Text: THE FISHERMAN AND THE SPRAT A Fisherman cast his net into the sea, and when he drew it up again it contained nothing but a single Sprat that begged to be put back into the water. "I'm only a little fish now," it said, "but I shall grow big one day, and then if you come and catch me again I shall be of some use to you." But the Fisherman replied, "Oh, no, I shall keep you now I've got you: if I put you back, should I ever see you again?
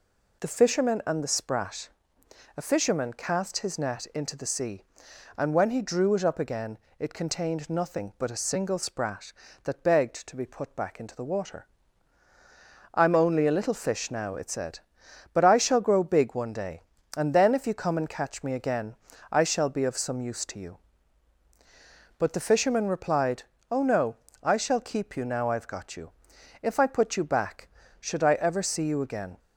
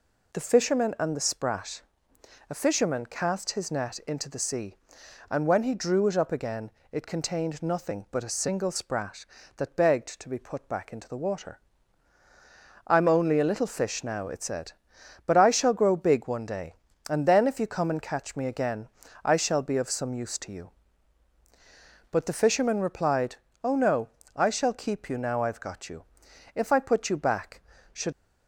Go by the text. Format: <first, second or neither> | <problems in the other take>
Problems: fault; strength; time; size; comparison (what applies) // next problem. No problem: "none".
first | pauses between "SPRAT" and "A"; noticeable; at 1.8 s; 0.70 s long; noticeable in the first // pauses between "again" and "it"; slight; at 6.6 s; 0.22 s long; slight in the first // pauses between "again" and "I"; at 18.8 s; 0.38 s long; also in the first // stops before "I ever see you again"; at 28.1 s